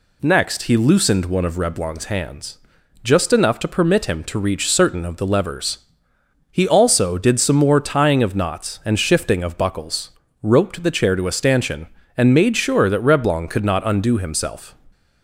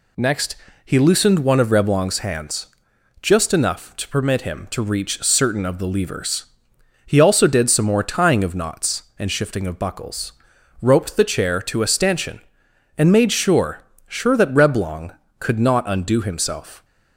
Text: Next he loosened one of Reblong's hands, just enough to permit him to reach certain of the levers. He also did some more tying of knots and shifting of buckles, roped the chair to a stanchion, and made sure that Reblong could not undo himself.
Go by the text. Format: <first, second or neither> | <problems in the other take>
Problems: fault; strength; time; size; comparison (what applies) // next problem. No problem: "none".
first | pauses between "Next" and "he"; slight; at 0.5 s; 0.30 s long // says "sure" twice; at 14.0 s